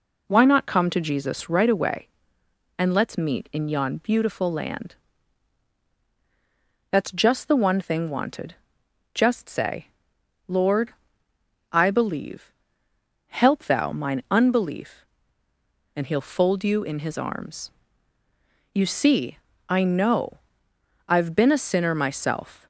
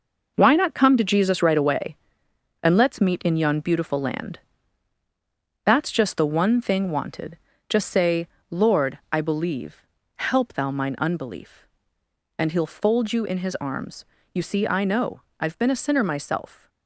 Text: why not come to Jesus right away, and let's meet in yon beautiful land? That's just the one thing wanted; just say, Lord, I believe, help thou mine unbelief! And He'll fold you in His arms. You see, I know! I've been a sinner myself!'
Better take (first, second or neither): first